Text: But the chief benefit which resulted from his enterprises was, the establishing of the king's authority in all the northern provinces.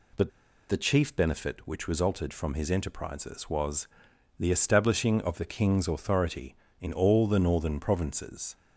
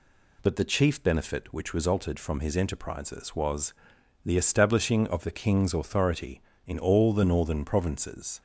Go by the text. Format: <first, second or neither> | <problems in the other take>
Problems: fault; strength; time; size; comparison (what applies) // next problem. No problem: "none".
second | pauses between "But" and "the"; at 0.3 s; 0.39 s long